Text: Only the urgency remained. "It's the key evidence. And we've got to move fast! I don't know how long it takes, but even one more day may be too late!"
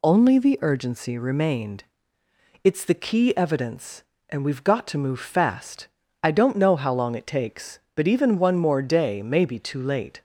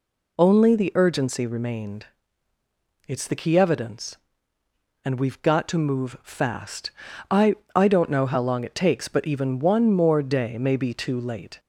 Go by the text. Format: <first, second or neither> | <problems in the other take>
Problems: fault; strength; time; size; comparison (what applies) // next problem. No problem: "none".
first | says "I" twice; at 7.7 s